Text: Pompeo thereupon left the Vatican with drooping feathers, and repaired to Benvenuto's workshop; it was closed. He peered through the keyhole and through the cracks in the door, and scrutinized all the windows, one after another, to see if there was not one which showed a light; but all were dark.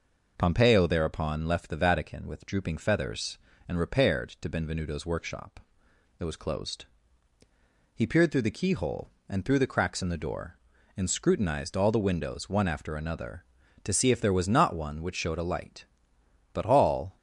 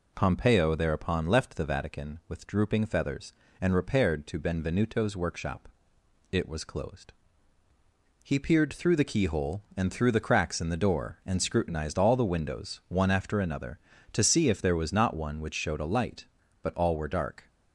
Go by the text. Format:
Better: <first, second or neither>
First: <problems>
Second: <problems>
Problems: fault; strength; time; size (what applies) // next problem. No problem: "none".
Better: second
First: stops before "were dark"; at 17.1 s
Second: none